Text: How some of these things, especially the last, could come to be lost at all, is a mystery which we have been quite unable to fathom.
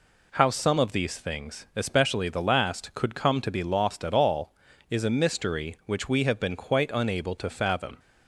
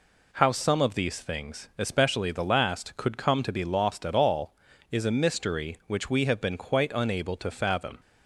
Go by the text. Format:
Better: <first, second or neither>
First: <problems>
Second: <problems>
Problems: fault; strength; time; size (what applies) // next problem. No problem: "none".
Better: neither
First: none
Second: none